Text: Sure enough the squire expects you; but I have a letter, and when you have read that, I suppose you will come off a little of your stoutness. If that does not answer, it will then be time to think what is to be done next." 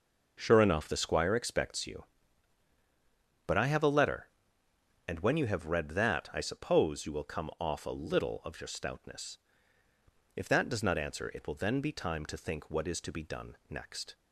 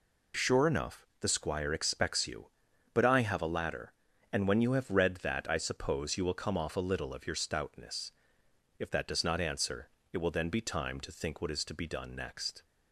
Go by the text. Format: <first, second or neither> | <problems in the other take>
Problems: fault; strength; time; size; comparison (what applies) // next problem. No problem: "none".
first | pauses between "enough" and "the"; slight; at 1.0 s; 0.16 s long // says "ladder" for "letter"; at 3.5 s